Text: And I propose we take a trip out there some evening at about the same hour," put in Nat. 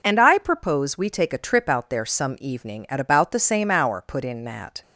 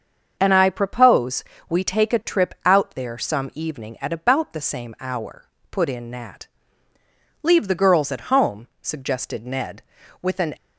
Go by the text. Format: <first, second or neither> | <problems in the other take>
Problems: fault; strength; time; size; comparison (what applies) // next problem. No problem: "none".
first | starts louder than the rest; until 1.4 s; 6.5 dB // pauses between "propose" and "we"; slight; at 1.4 s; 0.24 s long // goes on to say "Leave the girls at home suggested Ned with an"; strong; from 7.4 s on; 3.1 s long